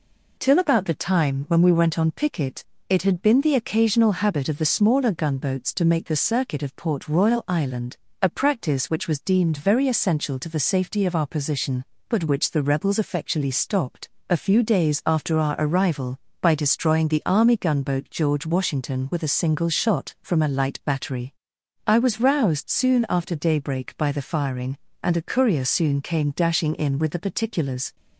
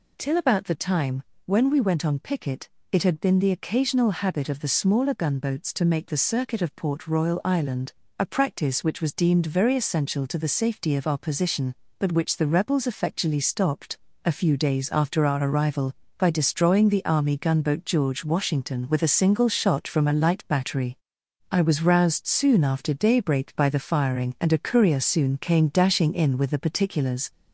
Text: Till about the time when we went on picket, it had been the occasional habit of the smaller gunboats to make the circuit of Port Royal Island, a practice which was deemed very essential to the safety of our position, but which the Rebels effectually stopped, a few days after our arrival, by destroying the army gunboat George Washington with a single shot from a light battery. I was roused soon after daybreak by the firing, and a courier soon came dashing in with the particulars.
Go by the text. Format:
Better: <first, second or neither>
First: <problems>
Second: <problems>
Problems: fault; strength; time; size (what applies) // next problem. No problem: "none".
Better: first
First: none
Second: gets louder; slight; throughout; 3 dB // pauses between "time" and "when"; slight; at 1.2 s; 0.22 s long